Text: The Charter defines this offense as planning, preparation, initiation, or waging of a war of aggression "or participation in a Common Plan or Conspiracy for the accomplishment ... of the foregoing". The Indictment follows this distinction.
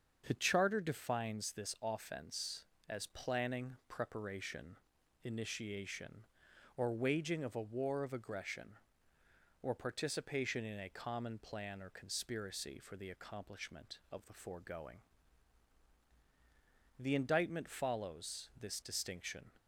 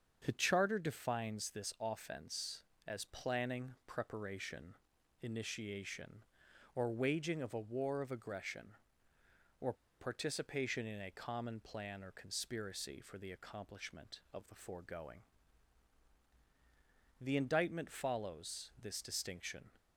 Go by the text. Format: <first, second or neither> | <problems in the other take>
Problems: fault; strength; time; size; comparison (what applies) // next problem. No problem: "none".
first | starts louder than the rest; until 1.2 s; 7 dB; also in the first // pauses between "or" and "participation"; slight; at 9.7 s; 0.26 s long